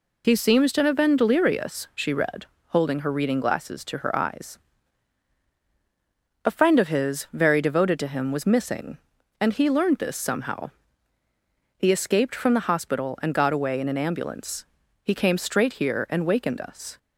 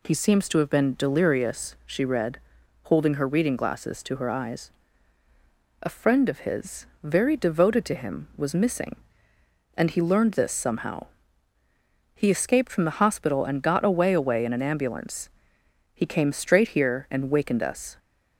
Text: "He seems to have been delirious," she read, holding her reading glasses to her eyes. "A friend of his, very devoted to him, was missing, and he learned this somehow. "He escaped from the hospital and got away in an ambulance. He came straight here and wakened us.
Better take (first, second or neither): first